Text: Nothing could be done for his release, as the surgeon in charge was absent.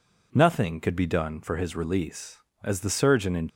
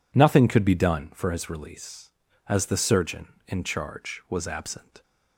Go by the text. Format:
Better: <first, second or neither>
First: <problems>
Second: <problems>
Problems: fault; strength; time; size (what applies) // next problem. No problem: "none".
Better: second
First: stops before "charge was absent"; at 3.4 s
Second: none